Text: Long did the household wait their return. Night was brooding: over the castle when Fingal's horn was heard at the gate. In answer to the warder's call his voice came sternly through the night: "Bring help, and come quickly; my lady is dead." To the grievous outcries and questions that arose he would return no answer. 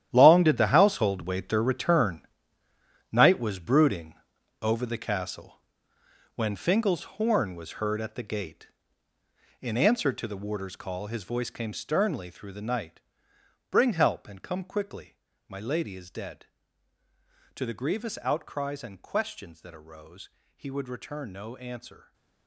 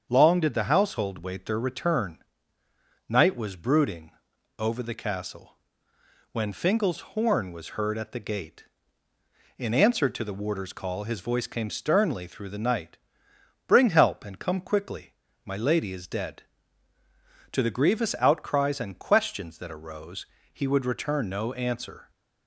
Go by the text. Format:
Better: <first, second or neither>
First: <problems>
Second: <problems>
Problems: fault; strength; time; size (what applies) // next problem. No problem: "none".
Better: second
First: gets quieter; strong; throughout; 14 dB // starts louder than the rest; strong; until 1.1 s; 11 dB // pauses between "castle" and "when"; noticeable; at 5.5 s; 0.80 s long // pauses between "Fingal's" and "horn"; slight; at 7.0 s; 0.16 s long // pauses between "arose" and "he"; slight; at 20.2 s; 0.26 s long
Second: starts louder than the rest; until 1.1 s; 7 dB // pauses between "castle" and "when"; noticeable; at 5.5 s; 0.80 s long // pauses between "Fingal's" and "horn"; slight; at 6.9 s; 0.16 s long // pauses between "arose" and "he"; slight; at 20.2 s; 0.26 s long